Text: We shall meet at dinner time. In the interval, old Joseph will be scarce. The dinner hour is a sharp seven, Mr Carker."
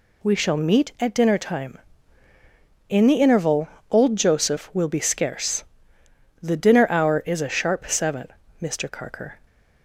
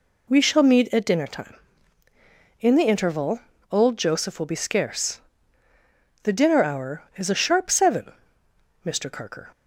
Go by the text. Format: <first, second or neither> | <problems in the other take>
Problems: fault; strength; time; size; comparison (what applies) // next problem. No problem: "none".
neither | none